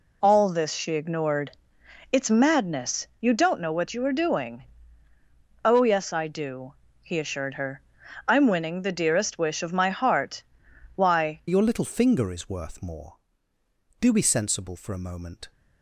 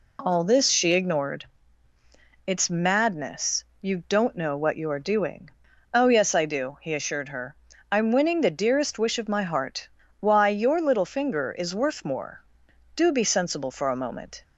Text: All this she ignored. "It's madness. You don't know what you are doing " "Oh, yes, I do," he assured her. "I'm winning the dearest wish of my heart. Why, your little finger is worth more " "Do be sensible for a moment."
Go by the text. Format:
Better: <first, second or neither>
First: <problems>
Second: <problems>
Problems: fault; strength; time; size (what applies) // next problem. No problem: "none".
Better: second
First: changes voice at "your"; from 11.4 s on; 4.1 s long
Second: none